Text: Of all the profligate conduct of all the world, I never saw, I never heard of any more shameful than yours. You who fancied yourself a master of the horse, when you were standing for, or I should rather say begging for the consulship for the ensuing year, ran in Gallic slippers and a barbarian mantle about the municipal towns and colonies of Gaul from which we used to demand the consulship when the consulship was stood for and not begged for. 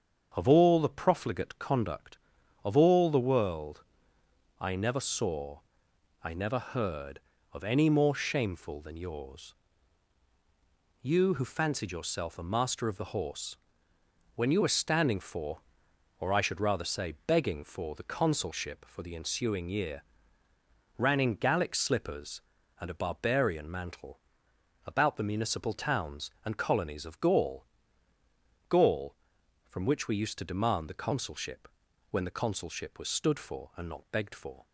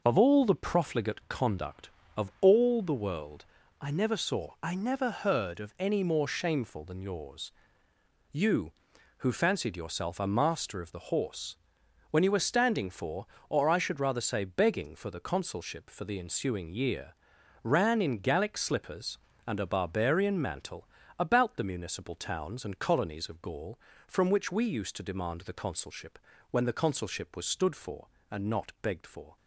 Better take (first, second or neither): second